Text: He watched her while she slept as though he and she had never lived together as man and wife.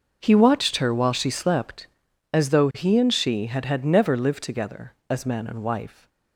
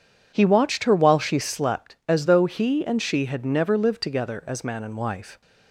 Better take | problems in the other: second | starts louder than the rest; noticeable; until 1.2 s; 6 dB // says "had" twice; at 3.6 s

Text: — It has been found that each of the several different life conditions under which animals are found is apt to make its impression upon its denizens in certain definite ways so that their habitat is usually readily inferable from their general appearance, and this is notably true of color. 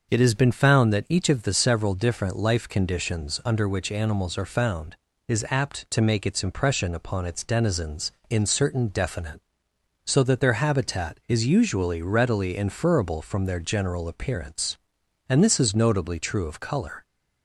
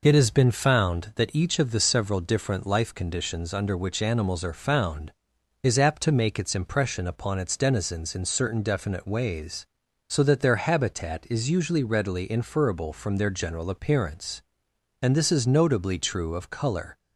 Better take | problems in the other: second | skips "ways"; at 9.7 s

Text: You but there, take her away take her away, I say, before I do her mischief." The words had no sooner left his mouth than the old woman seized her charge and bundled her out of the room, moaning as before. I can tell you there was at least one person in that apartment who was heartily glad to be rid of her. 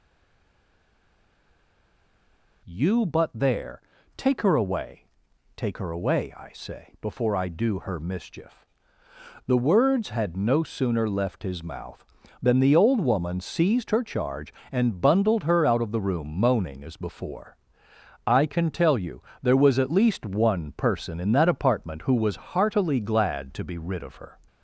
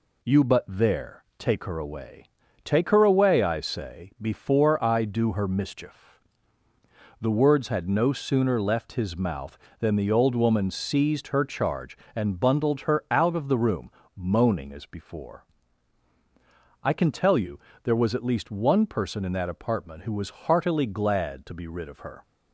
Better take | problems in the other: second | stays silent before the first word; strong; until 2.6 s; 2.6 s long // pauses between "away" and "take"; noticeable; at 5.0 s; 0.54 s long; also in the second // pauses between "you" and "there"; slight; at 19.2 s; 0.22 s long; slight in the second

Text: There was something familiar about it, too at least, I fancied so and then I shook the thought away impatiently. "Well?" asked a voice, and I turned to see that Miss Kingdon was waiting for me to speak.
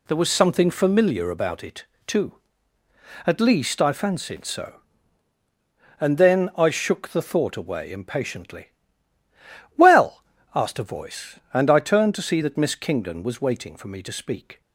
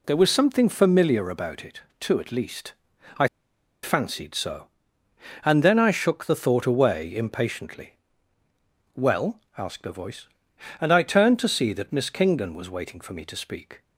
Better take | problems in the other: first | pauses between "I" and "fancied"; noticeable; at 3.2 s; 0.56 s long

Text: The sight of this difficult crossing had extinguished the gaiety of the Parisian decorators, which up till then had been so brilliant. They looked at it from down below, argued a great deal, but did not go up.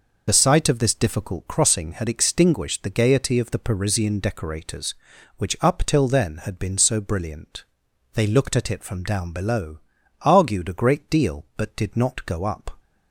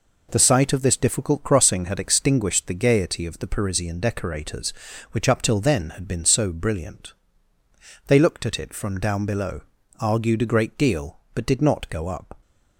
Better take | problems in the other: second | loses the start of "The"; at 0.2 s; 35 ms

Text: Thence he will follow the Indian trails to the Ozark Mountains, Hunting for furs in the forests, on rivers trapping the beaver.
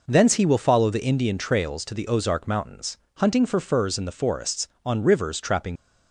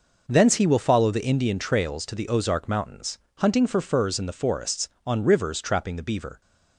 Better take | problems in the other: second | stops before "the beaver"; at 5.7 s

